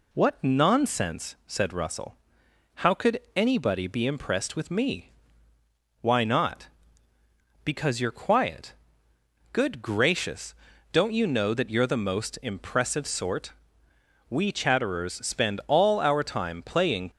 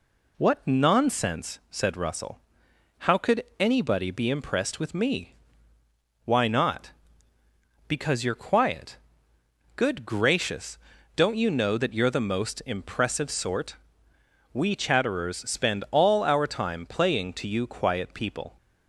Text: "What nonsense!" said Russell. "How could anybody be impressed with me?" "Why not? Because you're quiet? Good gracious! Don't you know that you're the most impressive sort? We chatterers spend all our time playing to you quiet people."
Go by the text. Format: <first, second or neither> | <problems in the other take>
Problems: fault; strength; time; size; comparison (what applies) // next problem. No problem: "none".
second | stops before "to you quiet people"; at 17.1 s